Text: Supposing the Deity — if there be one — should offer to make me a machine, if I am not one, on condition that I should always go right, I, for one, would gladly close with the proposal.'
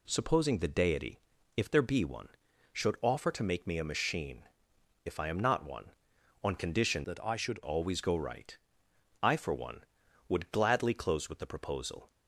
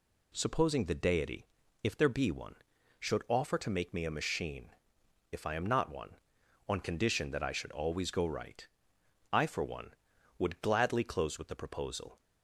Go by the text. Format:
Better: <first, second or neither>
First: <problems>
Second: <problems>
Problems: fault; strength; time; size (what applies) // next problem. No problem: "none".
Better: second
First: changes voice from "that" to "should"; from 7.0 to 7.6 s; 0.6 s long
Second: none